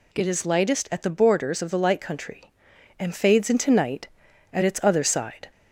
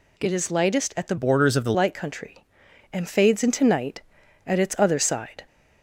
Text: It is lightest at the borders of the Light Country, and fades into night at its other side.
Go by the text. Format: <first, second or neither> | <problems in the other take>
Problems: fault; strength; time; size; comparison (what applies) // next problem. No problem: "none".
first | changes voice from "borders" to "the"; from 1.1 to 1.7 s; 0.6 s long